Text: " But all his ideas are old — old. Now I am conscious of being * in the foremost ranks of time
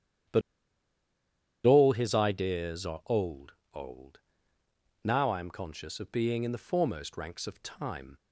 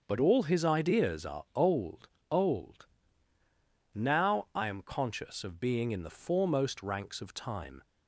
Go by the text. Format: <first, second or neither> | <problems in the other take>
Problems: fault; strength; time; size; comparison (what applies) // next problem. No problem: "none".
second | starts louder than the rest; strong; until 2.5 s; 10 dB; also in the second // pauses between "But" and "all"; at 0.4 s; 1.2 s long